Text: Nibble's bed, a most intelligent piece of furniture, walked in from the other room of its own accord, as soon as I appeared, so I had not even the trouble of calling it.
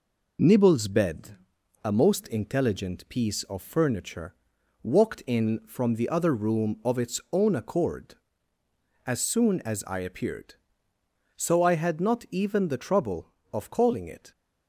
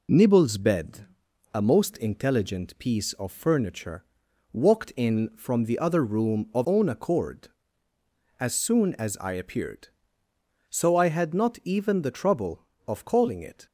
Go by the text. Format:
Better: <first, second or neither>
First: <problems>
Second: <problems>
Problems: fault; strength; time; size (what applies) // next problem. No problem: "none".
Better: first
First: none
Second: skips "its"; at 6.6 s